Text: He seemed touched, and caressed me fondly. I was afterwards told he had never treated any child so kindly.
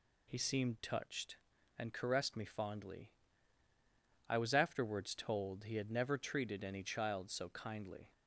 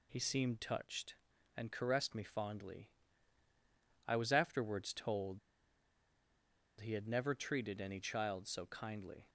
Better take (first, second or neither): first